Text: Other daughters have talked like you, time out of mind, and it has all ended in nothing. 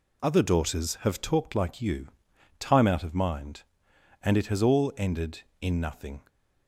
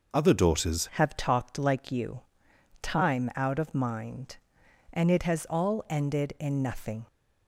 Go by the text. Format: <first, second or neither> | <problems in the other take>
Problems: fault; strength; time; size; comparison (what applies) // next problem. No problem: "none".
first | changes voice at "have"; from 0.9 s on; 6.1 s long